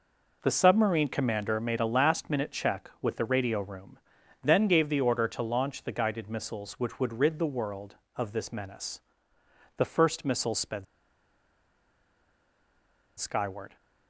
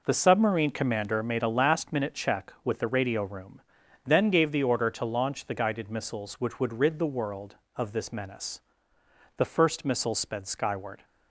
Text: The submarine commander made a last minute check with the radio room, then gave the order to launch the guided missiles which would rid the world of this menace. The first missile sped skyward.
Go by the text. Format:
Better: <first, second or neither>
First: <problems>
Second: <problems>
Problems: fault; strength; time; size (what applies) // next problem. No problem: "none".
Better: second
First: pauses between "sped" and "skyward"; strong; at 10.8 s; 2.3 s long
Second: none